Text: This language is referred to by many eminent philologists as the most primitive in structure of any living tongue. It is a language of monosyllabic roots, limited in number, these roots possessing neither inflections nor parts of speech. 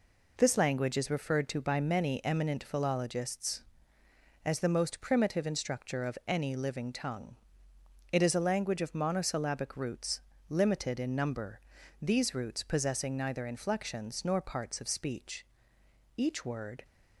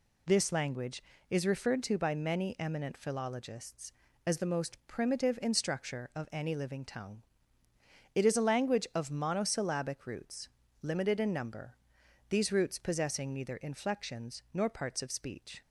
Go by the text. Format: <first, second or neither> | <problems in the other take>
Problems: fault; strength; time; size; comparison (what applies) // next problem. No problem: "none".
second | goes on to say "Each word"; noticeable; from 16.1 s on; 0.68 s long